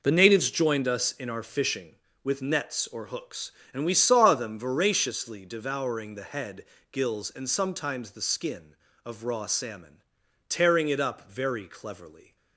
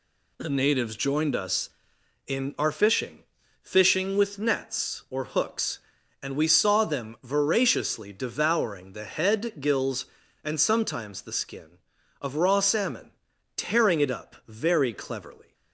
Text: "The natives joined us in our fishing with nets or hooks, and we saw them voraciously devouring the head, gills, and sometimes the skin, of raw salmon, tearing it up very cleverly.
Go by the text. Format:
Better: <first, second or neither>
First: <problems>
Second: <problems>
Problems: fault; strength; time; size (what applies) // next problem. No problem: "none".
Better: first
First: none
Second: says "fishing" twice; at 3.6 s